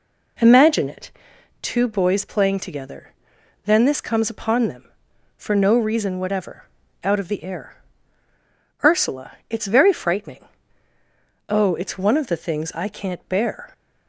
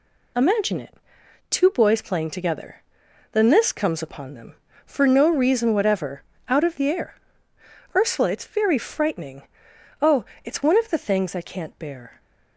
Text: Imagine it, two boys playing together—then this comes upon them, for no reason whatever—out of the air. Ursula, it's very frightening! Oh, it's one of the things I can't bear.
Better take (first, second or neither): second